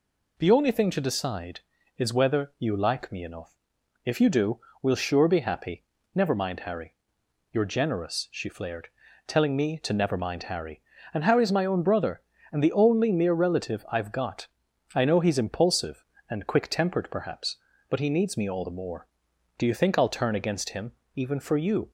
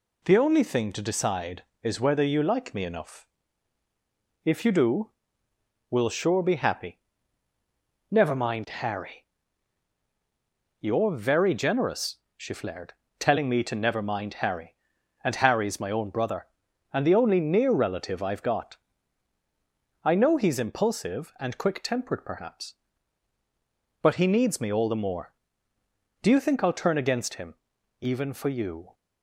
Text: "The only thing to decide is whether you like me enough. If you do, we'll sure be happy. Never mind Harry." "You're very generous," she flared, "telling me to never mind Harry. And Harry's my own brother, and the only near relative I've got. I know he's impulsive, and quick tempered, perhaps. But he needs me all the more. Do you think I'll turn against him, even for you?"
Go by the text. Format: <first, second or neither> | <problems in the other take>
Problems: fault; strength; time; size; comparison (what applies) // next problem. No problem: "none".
second | skips "very"; at 7.6 s